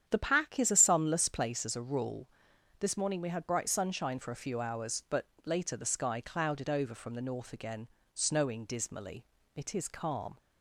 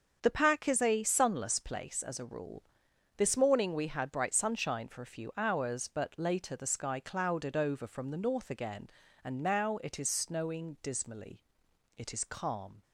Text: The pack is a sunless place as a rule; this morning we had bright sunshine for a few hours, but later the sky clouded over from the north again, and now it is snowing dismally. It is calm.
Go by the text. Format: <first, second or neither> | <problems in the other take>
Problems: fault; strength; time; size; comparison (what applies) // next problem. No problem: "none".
second | starts louder than the rest; strong; until 1.0 s; 9 dB; also in the second // pauses between "but" and "later"; slight; at 5.2 s; 0.16 s long // skips "and now it is"; at 8.0 s